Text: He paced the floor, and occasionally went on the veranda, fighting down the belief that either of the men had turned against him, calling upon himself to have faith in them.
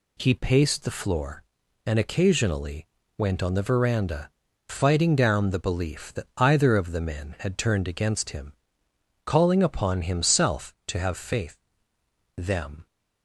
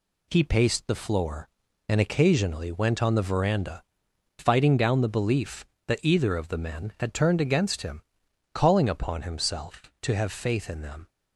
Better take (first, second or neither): second